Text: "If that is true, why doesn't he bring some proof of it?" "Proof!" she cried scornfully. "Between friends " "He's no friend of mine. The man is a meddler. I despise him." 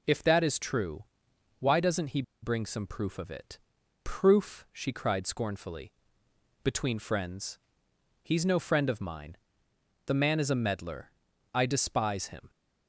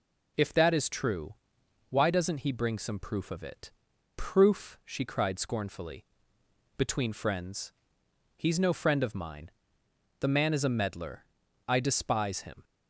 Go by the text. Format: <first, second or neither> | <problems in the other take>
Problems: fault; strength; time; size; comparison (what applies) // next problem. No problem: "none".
second | pauses between "he" and "bring"; slight; at 2.2 s; 0.20 s long